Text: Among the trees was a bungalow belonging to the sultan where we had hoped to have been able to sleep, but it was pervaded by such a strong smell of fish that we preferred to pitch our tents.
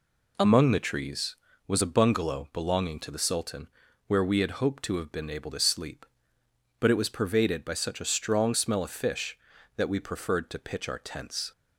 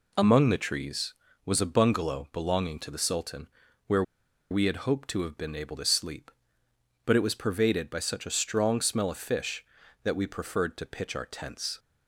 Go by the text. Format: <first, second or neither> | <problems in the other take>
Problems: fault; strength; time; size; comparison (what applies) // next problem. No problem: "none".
first | pauses between "sultan" and "where"; at 3.4 s; 0.40 s long; also in the first // pauses between "where" and "we"; noticeable; at 4.0 s; 0.48 s long